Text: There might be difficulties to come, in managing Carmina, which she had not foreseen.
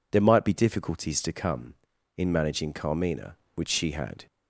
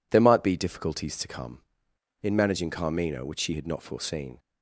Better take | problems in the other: second | stops before "not foreseen"; at 4.2 s

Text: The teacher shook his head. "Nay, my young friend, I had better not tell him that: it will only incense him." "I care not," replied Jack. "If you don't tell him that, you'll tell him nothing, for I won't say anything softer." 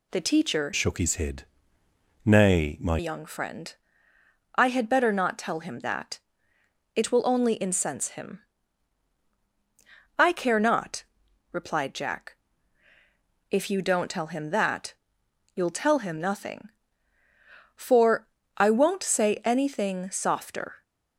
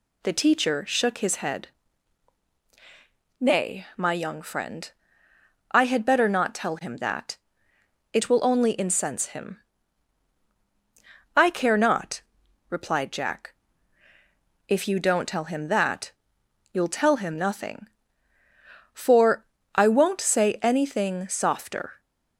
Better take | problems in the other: second | changes voice from "shook" to "my"; from 0.7 to 2.9 s; 2.2 s long // pauses between "for" and "I"; slight; at 18.2 s; 0.30 s long; slight in the second

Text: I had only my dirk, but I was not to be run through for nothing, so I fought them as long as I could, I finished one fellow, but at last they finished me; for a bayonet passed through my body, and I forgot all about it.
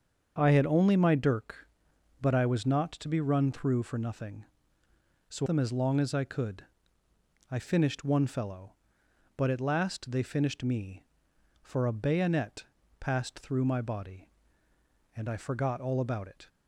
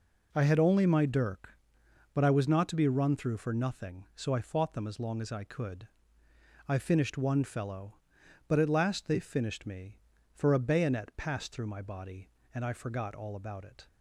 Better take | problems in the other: second | starts louder than the rest; until 1.3 s; 7 dB // skips "I fought"; at 5.4 s // pauses between "bayonet" and "passed"; slight; at 12.6 s; 0.36 s long

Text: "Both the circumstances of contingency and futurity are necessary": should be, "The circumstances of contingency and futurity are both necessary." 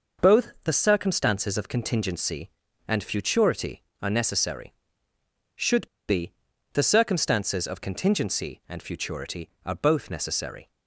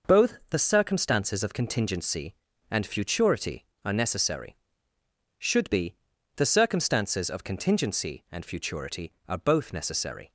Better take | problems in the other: second | pauses between "should" and "be"; slight; at 5.8 s; 0.22 s long

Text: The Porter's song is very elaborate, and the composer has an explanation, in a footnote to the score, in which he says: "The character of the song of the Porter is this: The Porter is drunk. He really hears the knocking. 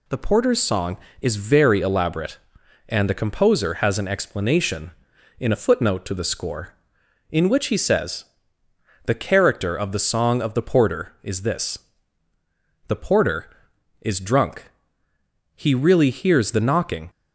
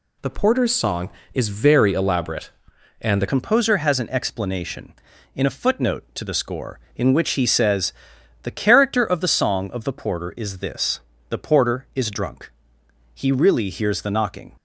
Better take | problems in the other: first | changes voice at "composer"; from 3.2 s on; 11.3 s long

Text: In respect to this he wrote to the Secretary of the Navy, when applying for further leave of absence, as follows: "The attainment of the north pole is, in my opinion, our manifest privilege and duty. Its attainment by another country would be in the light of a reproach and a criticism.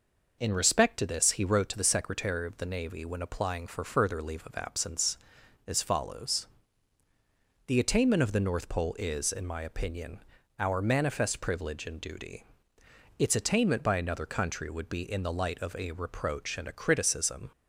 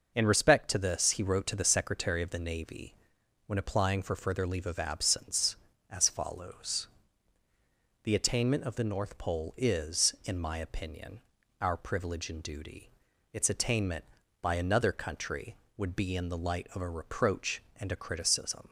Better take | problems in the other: first | skips "manifest"; at 11.7 s

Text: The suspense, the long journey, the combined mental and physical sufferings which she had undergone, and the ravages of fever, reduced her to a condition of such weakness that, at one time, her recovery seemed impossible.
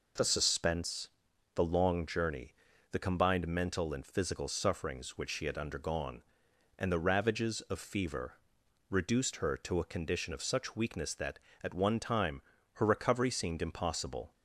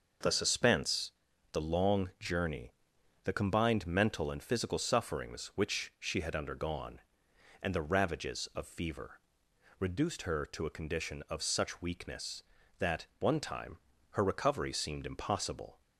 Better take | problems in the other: first | skips "at"; at 13.1 s

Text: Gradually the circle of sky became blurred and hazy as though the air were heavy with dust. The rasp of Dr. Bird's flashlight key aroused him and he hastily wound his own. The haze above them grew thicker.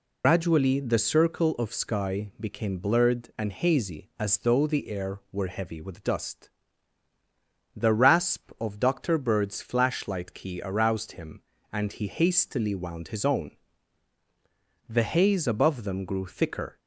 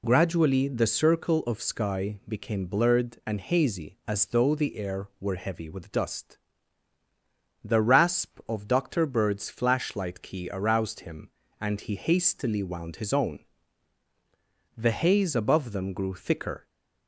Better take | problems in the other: second | loses the start of "Gradually"; at 0.2 s; 95 ms

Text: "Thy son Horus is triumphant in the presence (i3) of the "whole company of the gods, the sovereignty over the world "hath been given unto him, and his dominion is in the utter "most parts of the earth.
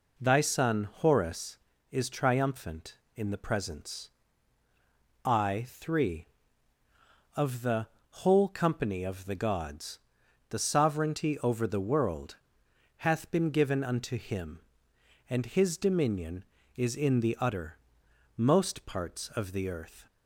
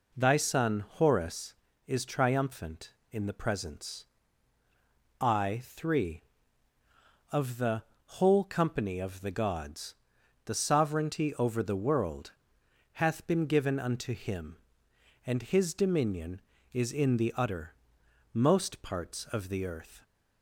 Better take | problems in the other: neither | pauses between "the" and "whole"; slight; the same in both // pauses between "world" and "hath"; noticeable; the same in both // pauses between "utter" and "most"; noticeable; the same in both

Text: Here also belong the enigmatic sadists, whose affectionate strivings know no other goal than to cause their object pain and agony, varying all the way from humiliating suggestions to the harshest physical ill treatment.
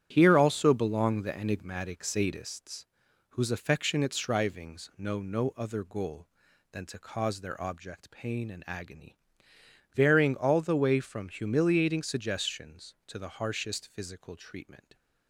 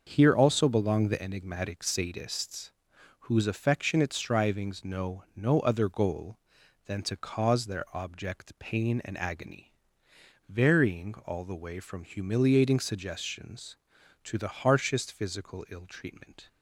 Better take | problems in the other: second | starts louder than the rest; strong; until 1.1 s; 9.5 dB; also in the second // skips "ill"; at 14.3 s

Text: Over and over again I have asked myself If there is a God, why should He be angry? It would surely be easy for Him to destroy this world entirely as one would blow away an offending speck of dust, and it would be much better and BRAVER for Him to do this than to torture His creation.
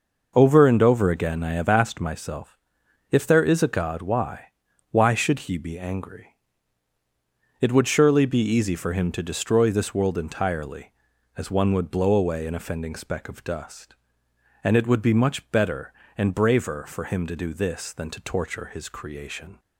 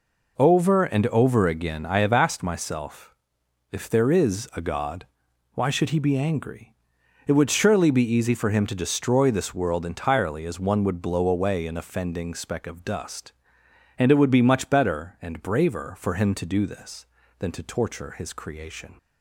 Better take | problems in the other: second | pauses between "myself" and "If"; noticeable; at 2.5 s; 0.54 s long; noticeable in the second // says "why" twice; at 4.8 s

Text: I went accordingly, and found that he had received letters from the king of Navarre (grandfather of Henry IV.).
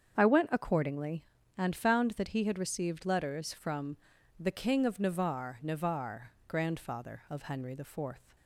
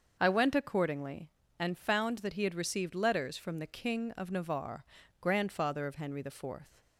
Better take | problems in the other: second | starts louder than the rest; strong; until 1.2 s; 7.5 dB; also in the second // pauses between "from" and "the"; at 3.9 s; 0.42 s long // says "Navarre" twice; at 5.6 s

